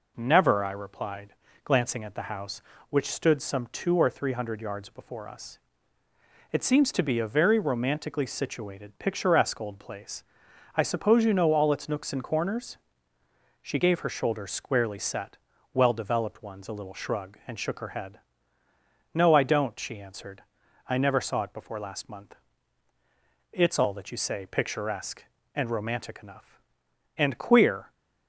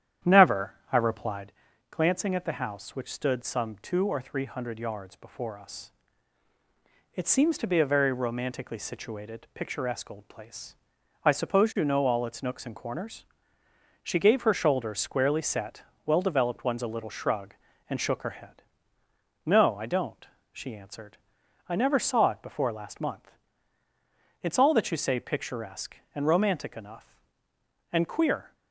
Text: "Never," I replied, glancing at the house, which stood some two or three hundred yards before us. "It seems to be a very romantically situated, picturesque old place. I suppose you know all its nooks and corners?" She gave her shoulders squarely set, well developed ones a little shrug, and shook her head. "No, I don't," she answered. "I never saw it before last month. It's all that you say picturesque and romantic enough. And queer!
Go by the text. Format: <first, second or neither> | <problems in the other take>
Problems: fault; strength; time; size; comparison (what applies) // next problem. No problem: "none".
first | starts louder than the rest; strong; until 1.6 s; 10 dB